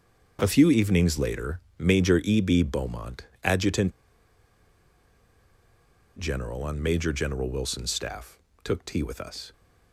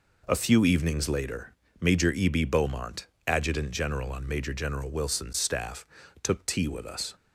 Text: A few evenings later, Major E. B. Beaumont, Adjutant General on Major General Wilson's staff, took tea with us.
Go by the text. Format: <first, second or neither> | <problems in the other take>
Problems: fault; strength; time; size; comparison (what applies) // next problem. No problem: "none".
second | starts louder than the rest; until 1.4 s; 6.5 dB // pauses between "Adjutant" and "General"; strong; at 3.9 s; 2.2 s long